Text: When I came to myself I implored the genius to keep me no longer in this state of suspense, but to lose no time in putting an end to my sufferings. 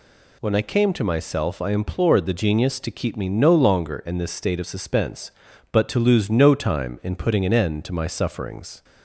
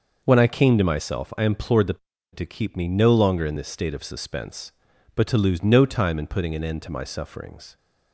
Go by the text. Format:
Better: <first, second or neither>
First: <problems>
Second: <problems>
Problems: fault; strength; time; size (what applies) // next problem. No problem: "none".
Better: first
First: none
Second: skips "genius"; at 2.1 s